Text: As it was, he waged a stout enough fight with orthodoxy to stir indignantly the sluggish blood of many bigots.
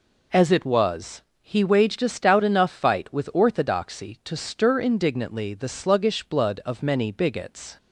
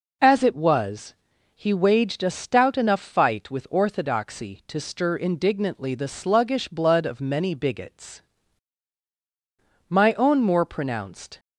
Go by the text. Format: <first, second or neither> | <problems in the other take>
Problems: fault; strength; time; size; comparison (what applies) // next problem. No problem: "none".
first | goes on to say "My own more pronounced"; from 9.8 s on; 1.5 s long